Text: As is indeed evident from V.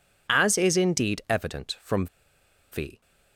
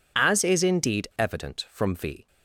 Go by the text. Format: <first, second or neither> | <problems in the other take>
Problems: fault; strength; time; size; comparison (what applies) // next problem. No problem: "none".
second | pauses between "from" and "V"; noticeable; at 2.0 s; 0.66 s long